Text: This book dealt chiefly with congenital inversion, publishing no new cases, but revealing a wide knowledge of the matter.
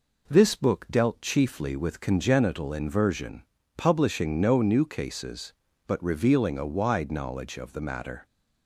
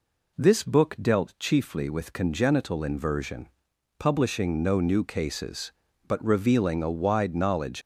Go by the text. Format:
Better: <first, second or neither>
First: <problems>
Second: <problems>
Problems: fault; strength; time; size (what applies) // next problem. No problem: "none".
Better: first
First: none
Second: stops before "of the matter"; at 7.8 s